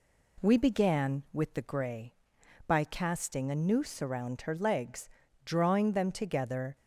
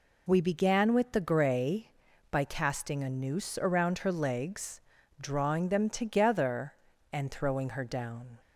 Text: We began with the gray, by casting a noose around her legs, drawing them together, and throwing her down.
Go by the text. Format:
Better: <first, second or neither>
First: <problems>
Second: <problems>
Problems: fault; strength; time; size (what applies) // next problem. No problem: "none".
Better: second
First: stops before "and throwing her down"; at 6.7 s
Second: none